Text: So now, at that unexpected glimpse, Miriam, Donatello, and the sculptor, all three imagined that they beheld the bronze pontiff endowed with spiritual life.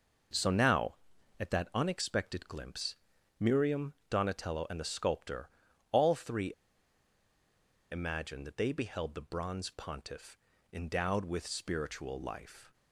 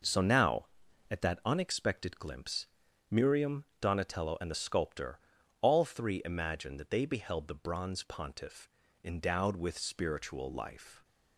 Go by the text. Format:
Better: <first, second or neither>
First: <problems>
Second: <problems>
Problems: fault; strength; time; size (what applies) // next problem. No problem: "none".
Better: second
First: pauses between "three" and "imagined"; strong; at 6.5 s; 1.4 s long // pauses between "pontiff" and "endowed"; slight; at 10.3 s; 0.34 s long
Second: pauses between "pontiff" and "endowed"; slight; at 8.6 s; 0.34 s long